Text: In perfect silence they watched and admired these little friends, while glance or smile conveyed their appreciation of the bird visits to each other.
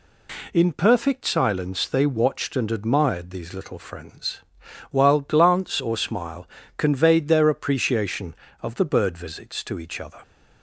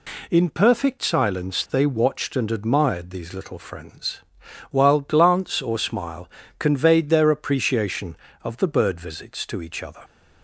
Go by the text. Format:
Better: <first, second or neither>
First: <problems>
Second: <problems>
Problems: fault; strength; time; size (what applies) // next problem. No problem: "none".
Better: neither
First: pauses between "smile" and "conveyed"; slight; at 6.4 s; 0.30 s long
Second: pauses between "smile" and "conveyed"; slight; at 6.2 s; 0.30 s long